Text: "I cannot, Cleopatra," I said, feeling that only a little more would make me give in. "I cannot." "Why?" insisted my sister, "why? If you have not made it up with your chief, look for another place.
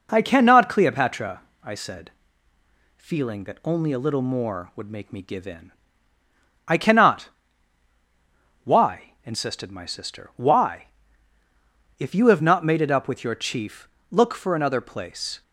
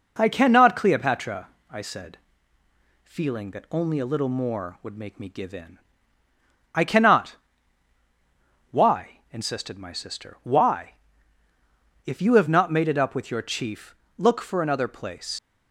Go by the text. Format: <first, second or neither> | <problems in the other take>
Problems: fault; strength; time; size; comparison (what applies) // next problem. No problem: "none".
first | leaves "place" unfinished; at 15.3 s; 100 ms